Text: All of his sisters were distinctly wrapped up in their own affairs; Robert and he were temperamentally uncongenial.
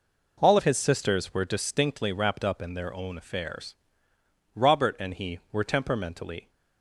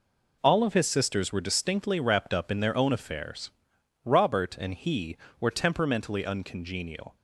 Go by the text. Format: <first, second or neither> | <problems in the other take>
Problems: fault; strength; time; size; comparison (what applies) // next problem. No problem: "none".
second | stops before "uncongenial"; at 6.4 s